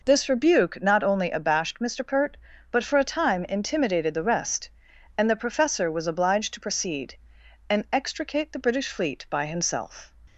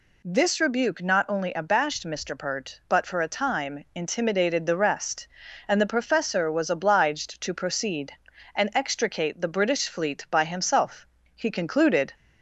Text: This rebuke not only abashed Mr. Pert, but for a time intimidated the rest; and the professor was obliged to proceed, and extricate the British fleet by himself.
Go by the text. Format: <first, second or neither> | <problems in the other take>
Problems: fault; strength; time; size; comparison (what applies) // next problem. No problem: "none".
first | goes on to say "He concluded"; noticeable; from 11.3 s on; 0.78 s long